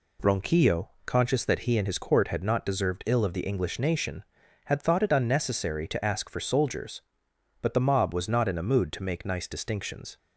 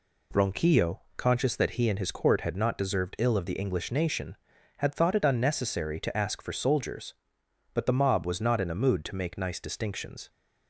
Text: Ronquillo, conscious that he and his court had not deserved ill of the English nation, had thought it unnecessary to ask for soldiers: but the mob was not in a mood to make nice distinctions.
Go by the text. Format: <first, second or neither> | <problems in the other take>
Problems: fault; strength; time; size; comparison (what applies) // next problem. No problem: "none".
neither | none